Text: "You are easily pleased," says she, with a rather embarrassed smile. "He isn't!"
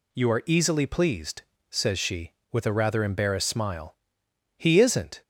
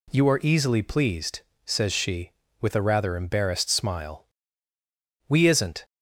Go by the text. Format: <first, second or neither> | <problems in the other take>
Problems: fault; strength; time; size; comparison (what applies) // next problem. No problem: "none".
first | says "We" for "He"; at 5.2 s